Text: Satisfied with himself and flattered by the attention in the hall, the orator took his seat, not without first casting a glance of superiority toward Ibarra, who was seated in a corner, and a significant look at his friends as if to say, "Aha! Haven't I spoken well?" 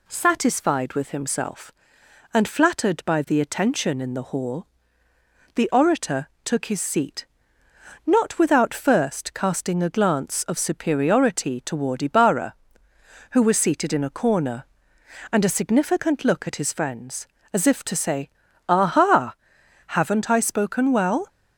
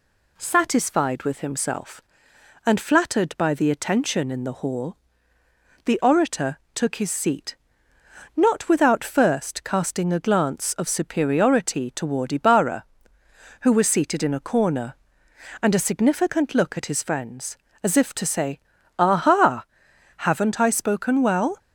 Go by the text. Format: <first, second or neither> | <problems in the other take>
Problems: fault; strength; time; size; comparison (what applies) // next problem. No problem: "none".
neither | pauses between "orator" and "took"; slight; the same in both